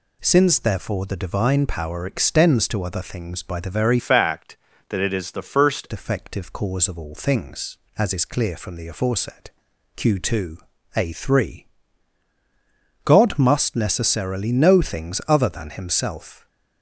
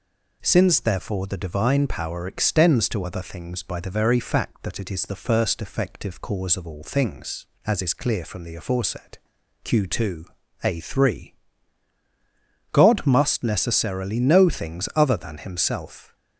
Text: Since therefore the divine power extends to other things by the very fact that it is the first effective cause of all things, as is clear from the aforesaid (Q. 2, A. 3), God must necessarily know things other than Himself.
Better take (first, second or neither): second